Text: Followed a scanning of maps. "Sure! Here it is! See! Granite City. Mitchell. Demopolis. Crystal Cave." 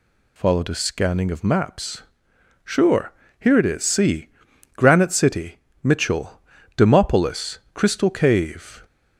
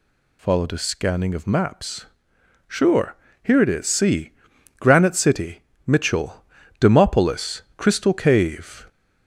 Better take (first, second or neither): first